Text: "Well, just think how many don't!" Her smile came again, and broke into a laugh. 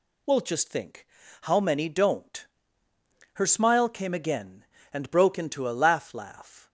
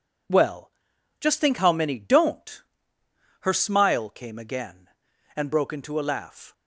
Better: second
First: pauses between "think" and "how"; slight; at 1.0 s; 0.34 s long // says "laugh" twice; at 6.1 s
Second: none

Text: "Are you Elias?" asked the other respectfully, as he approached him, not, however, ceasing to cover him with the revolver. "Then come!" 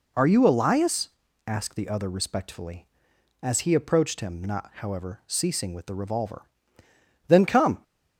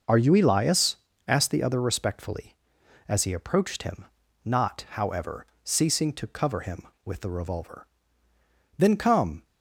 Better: second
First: skips "to cover him"; at 5.7 s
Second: none

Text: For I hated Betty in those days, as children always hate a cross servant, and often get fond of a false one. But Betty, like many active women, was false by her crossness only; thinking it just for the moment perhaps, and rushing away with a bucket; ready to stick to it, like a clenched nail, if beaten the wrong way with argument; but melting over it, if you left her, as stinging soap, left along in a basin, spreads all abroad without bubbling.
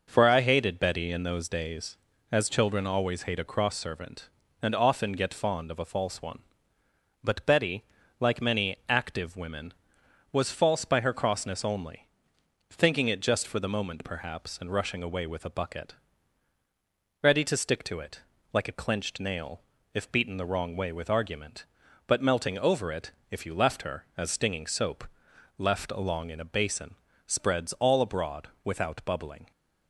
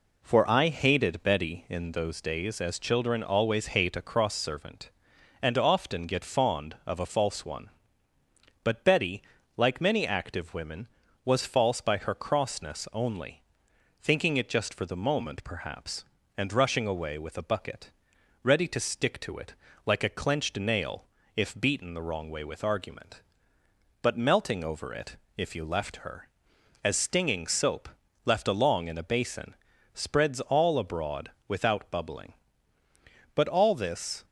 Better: first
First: pauses between "abroad" and "without"; slight; at 28.4 s; 0.18 s long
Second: pauses between "abroad" and "without"; slight; at 31.3 s; 0.16 s long // goes on to say "But all this"; noticeable; from 33.3 s on; 0.90 s long

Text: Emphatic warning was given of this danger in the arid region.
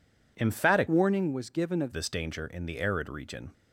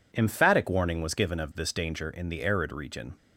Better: second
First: changes voice from "warning" to "of"; from 0.8 to 1.9 s; 1.1 s long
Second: none

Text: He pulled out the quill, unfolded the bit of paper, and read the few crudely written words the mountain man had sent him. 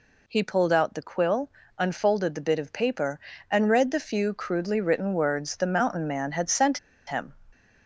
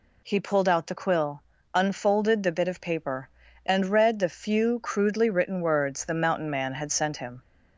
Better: second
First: pauses between "sent" and "him"; slight; at 6.7 s; 0.29 s long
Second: none

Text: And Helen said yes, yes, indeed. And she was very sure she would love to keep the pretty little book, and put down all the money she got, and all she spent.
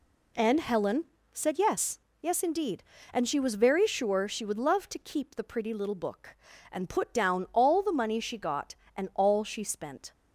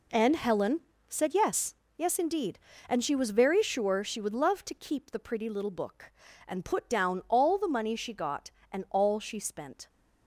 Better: first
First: pauses between "Helen" and "said"; slight; at 1.0 s; 0.28 s long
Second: gets quieter; strong; throughout; 10 dB // pauses between "Helen" and "said"; slight; at 0.8 s; 0.28 s long

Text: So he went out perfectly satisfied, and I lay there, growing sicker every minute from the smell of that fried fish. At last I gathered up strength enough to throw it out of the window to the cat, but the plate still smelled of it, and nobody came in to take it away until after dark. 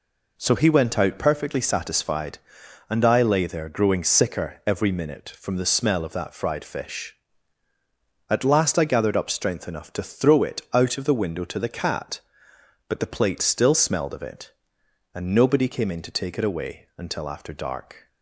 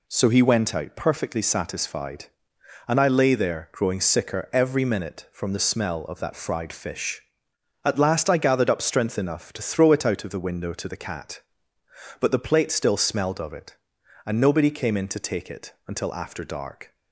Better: first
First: none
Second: skips "away"; at 15.7 s

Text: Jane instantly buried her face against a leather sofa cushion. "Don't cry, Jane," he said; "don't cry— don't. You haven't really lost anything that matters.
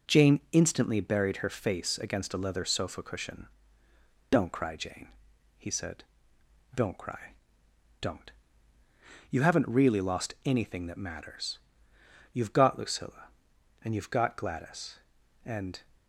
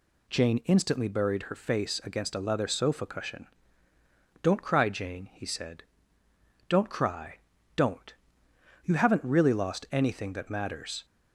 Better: second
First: goes on to say "You've got Lucilla and you've got Gladys and"; strong; from 12.3 s on; 3.4 s long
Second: none

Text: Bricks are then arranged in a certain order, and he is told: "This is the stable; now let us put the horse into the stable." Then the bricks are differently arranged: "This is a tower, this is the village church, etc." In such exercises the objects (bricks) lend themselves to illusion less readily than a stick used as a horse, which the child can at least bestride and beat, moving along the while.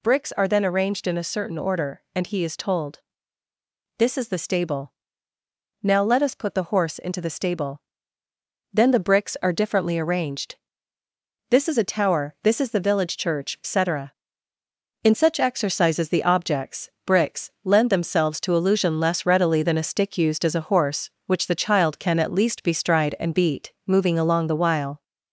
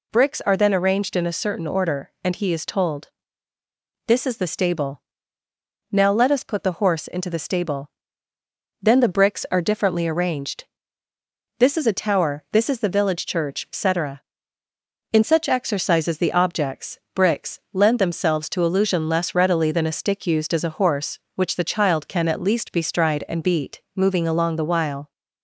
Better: second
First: gets louder; slight; throughout; 2.5 dB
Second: none

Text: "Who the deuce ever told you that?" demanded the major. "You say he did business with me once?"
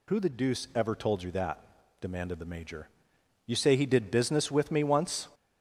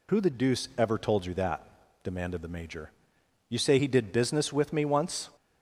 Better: second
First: gets louder; noticeable; throughout; 6 dB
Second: none

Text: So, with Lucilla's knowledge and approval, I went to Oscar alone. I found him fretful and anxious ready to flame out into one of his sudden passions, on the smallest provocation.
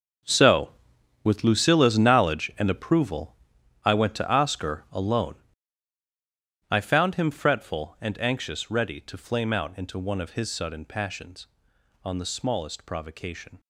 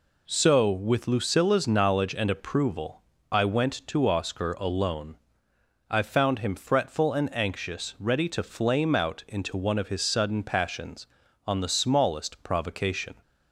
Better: second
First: gets quieter; strong; throughout; 13.5 dB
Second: none

